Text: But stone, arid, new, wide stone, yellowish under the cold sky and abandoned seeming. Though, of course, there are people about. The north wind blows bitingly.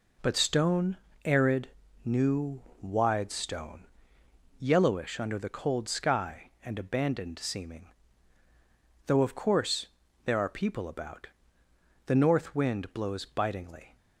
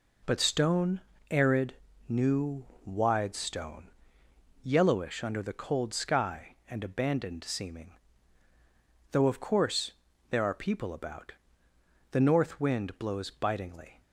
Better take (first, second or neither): neither